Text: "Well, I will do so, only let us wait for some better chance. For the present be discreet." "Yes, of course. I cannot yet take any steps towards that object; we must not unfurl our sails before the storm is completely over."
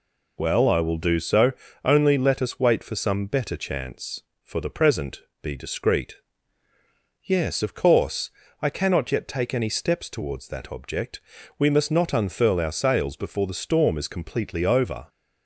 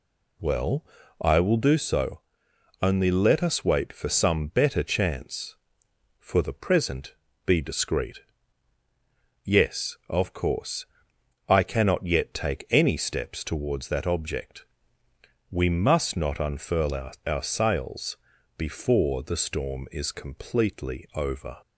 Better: first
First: pauses between "present" and "be"; slight; at 5.2 s; 0.20 s long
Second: pauses between "present" and "be"; slight; at 7.1 s; 0.32 s long // says "our" twice; at 17.2 s // pauses between "sails" and "before"; at 18.1 s; 0.42 s long

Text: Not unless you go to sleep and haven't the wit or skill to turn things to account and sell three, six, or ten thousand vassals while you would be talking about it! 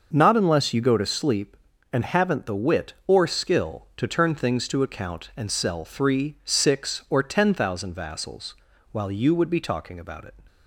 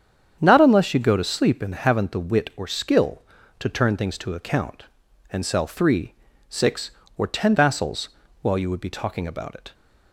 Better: first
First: starts louder than the rest; until 1.1 s; 6 dB // pauses between "vassals" and "while"; slight; at 8.5 s; 0.36 s long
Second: starts louder than the rest; strong; until 1.4 s; 8 dB // skips "thousand"; at 7.5 s // pauses between "vassals" and "while"; slight; at 8.0 s; 0.32 s long

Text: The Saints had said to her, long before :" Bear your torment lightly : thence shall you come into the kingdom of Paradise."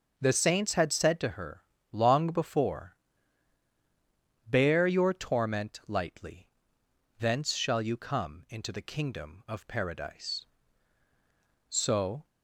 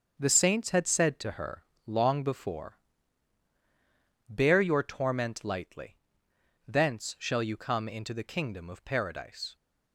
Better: second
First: goes on to say "So"; from 11.6 s on; 0.56 s long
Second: none

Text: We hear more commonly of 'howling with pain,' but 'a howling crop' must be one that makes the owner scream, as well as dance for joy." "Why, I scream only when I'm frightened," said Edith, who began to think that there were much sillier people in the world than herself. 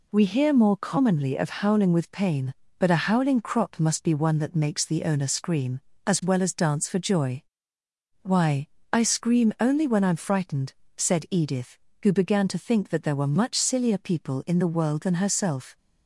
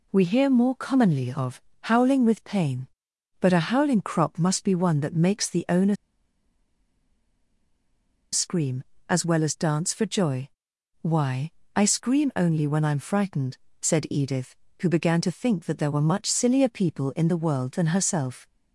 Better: first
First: none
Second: pauses between "of" and "howling"; slight; at 1.6 s; 0.22 s long // pauses between "owner" and "scream"; strong; at 5.9 s; 2.3 s long

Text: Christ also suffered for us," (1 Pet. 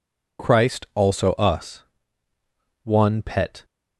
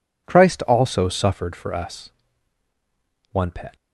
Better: second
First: skips "suffered for"; at 1.3 s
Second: none

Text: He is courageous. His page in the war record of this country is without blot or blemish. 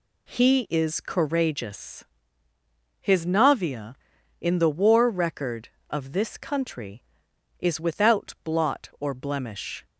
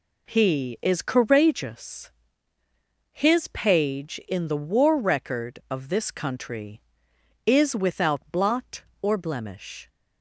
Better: second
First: says "navia" for "page"; at 3.2 s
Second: none

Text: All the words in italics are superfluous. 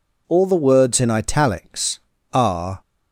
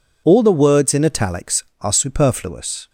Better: second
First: stops before "superfluous"; at 2.8 s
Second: none

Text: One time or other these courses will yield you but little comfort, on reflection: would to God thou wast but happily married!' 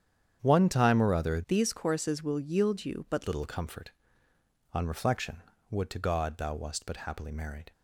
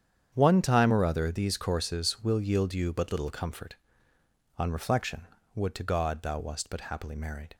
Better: second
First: starts louder than the rest; strong; until 1.4 s; 8.5 dB // changes voice from "these" to "but"; from 1.4 to 3.2 s; 1.8 s long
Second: starts louder than the rest; strong; until 1.3 s; 8.5 dB

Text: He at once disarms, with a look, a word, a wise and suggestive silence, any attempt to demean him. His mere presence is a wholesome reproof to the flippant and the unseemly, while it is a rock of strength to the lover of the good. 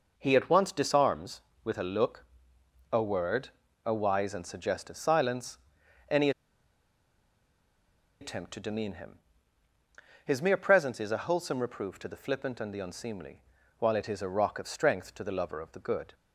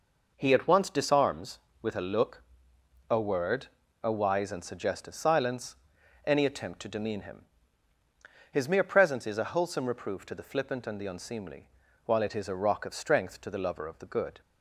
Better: second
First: pauses between "any" and "attempt"; strong; at 6.3 s; 1.9 s long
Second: none

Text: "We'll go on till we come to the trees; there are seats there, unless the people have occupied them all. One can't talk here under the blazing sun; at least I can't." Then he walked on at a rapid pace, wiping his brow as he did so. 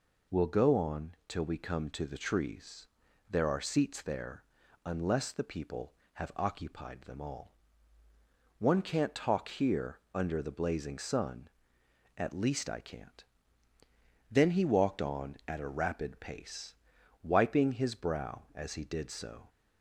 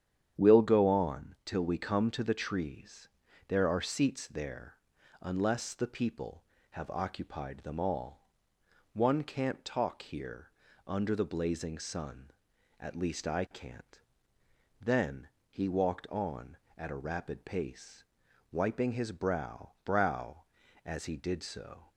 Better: first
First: pauses between "here" and "under"; slight; at 9.9 s; 0.16 s long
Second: starts louder than the rest; strong; until 1.5 s; 9 dB // pauses between "here" and "under"; slight; at 10.5 s; 0.34 s long // pauses between "Then" and "he"; slight; at 15.2 s; 0.22 s long // says "brow" twice; at 19.8 s

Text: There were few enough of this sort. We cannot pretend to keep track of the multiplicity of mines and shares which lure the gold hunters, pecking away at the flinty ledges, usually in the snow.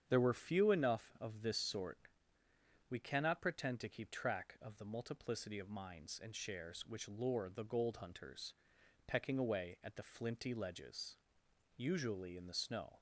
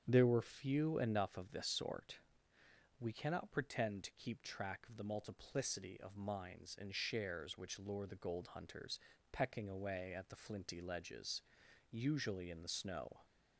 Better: neither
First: starts louder than the rest; strong; until 1.0 s; 8 dB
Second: starts louder than the rest; strong; until 1.0 s; 8 dB

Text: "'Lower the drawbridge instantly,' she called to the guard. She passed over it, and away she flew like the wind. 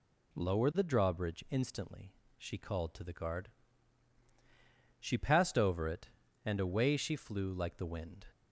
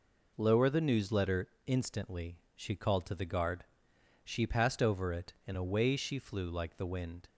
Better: first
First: none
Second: says "newsletter" for "drawbridge"; at 0.8 s

